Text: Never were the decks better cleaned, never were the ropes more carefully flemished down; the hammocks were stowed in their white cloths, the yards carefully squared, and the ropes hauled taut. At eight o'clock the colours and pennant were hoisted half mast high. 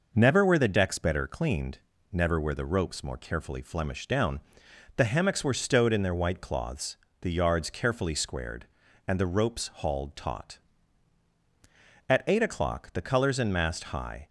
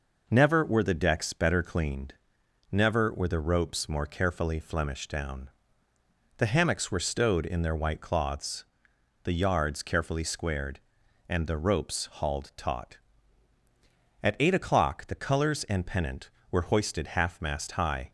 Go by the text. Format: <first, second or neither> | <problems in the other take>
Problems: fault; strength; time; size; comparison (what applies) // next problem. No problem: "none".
second | skips "pennant were hoisted half"; at 13.5 s